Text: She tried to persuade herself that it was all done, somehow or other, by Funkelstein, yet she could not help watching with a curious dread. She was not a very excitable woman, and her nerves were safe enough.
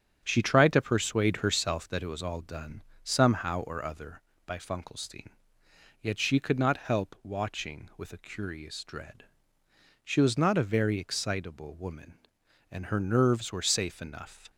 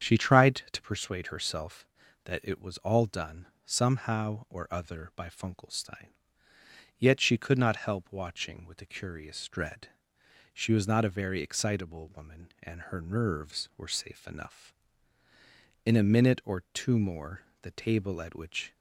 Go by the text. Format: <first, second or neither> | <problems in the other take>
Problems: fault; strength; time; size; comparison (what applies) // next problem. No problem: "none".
first | starts louder than the rest; strong; until 1.1 s; 8 dB; strong in the first // goes on to say "In a minute or two more the table at which"; strong; from 15.8 s on; 2.8 s long